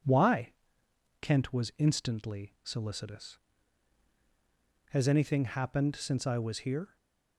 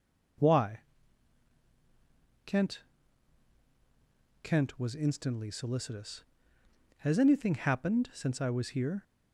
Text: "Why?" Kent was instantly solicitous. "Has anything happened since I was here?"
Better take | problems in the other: first | says "Kent" twice; at 4.4 s

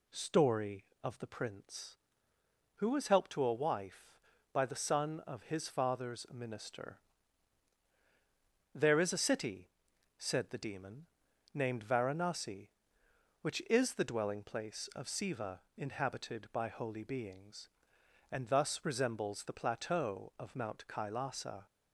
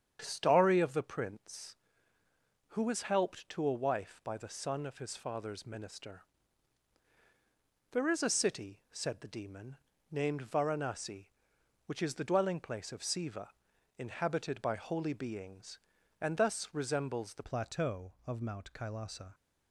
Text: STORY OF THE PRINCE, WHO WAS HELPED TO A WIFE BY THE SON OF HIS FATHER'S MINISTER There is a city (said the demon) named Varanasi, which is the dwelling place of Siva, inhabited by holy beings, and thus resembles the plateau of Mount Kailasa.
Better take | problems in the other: first | starts louder than the rest; strong; until 1.2 s; 8.5 dB // pauses between "MINISTER" and "There"; strong; at 6.2 s; 1.6 s long; strong in the first // changes voice at "plateau"; from 17.4 s on; 1.9 s long

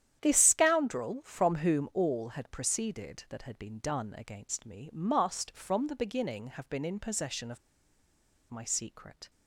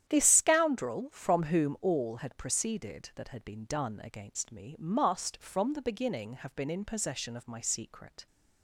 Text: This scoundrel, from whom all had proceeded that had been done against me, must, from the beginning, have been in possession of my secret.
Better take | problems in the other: second | starts louder than the rest; strong; until 1.2 s; 10.5 dB; strong in the second // pauses between "of" and "my"; noticeable; at 7.5 s; 0.90 s long

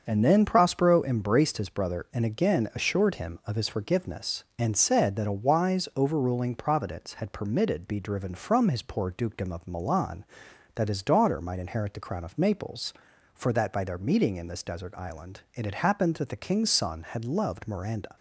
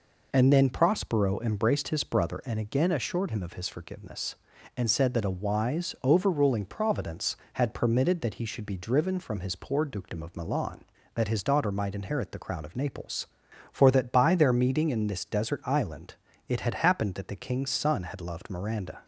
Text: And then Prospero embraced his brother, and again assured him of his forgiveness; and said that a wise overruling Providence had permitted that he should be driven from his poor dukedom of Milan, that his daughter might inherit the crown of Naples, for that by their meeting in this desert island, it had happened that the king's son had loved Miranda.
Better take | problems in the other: second | starts louder than the rest; until 1.0 s; 7 dB // skips "that he should"; at 7.8 s

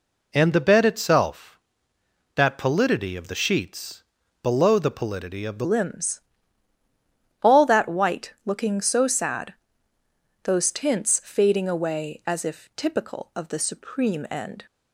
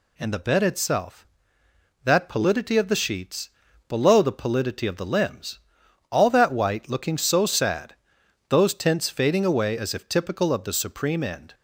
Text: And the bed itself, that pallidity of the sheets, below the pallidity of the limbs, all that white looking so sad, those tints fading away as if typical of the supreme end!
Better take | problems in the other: second | changes voice at "limbs"; from 5.6 s on; 9.0 s long

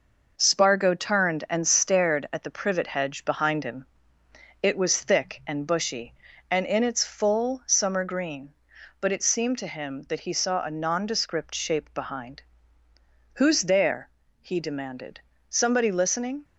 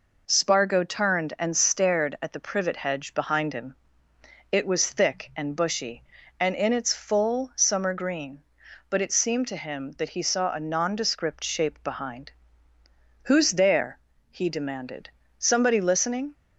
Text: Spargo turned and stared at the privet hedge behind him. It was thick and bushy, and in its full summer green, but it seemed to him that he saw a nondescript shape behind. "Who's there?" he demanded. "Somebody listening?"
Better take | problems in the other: second | gets quieter; noticeable; throughout; 4.5 dB

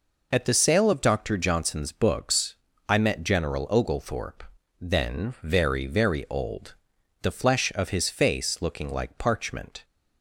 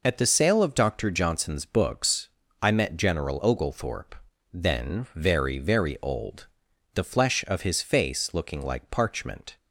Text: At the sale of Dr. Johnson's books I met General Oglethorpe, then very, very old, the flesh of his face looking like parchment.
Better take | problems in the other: neither | pauses between "books" and "I"; slight; the same in both

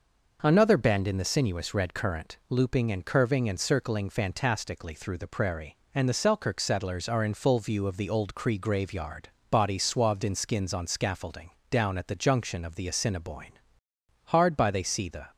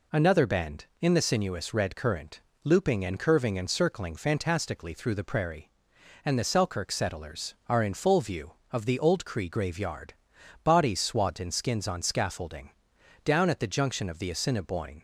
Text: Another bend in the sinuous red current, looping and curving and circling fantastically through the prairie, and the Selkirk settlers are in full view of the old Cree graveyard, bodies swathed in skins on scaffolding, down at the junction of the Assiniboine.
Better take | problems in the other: second | goes on to say "Hard by they see the"; noticeable; from 14.2 s on; 1.0 s long

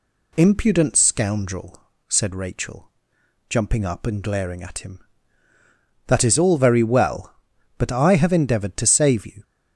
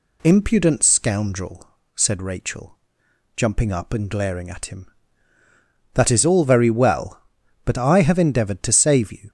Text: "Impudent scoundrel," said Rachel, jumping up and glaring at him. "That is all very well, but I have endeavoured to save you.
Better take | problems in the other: neither | none

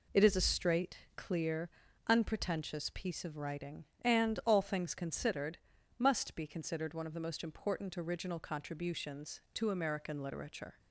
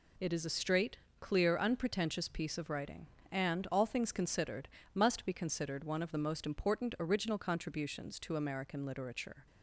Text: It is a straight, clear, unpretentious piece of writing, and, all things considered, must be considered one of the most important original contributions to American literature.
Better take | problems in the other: neither | none

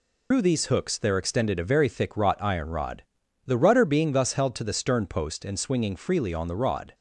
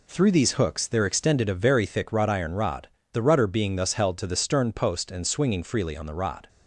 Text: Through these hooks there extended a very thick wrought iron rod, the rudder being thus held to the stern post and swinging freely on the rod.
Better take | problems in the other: second | loses the start of "Through"; at 0.3 s; 120 ms

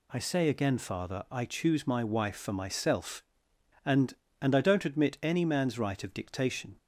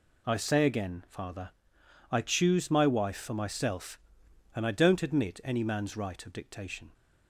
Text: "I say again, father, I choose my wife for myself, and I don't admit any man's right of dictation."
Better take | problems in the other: second | says "and" twice; at 4.3 s

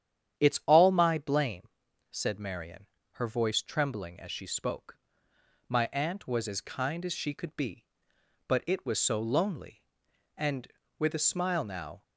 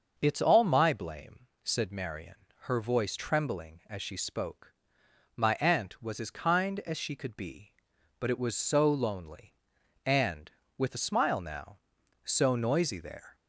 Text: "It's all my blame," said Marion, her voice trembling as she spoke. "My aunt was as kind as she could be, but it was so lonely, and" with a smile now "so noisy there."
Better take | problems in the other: second | starts louder than the rest; strong; until 1.4 s; 9.5 dB; noticeable in the second // stops before "so noisy there"; at 12.0 s

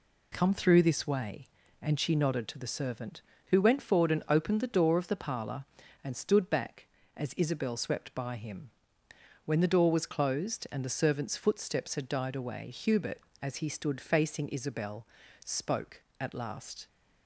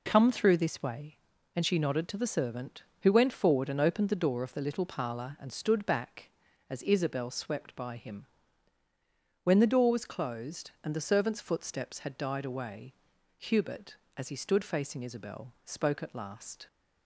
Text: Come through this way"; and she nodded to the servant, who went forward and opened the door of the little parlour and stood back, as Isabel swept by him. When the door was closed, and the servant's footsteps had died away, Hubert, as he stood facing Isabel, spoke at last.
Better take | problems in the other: second | skips "little"; at 5.1 s

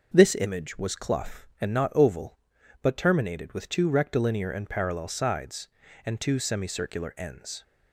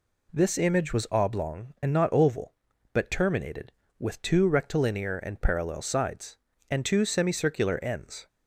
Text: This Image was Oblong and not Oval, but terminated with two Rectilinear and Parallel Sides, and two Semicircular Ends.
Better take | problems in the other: second | says "Clough" for "Oblong"; at 0.9 s

